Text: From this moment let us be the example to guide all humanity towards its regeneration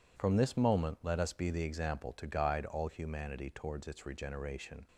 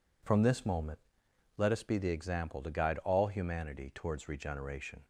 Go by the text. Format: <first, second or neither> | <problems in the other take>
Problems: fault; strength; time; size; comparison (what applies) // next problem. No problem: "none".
first | pauses between "moment" and "let"; noticeable; at 0.9 s; 0.58 s long // skips "its"; at 4.2 s